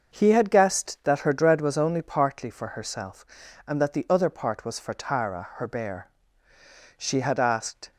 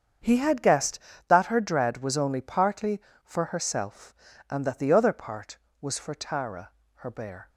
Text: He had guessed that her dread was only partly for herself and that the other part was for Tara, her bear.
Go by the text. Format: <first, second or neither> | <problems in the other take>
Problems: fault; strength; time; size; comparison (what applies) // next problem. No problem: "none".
second | starts louder than the rest; until 1.1 s; 6 dB; strong in the second // goes on to say "She had asked"; noticeable; from 6.9 s on; 0.94 s long